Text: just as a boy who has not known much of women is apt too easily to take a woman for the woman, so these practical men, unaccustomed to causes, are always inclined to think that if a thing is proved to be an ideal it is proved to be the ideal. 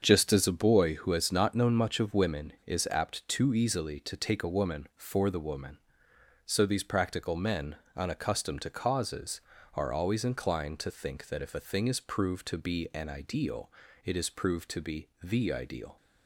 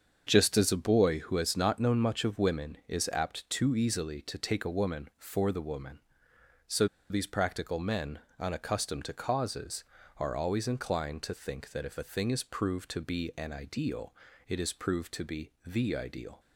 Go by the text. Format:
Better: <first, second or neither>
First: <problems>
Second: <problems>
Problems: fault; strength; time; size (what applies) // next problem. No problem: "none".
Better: first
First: starts louder than the rest; until 1.0 s; 7 dB // pauses between "ideal" and "it"; slight; at 13.6 s; 0.36 s long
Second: starts louder than the rest; until 1.2 s; 7 dB // pauses between "so" and "these"; slight; at 6.8 s; 0.24 s long // pauses between "ideal" and "it"; slight; at 14.1 s; 0.36 s long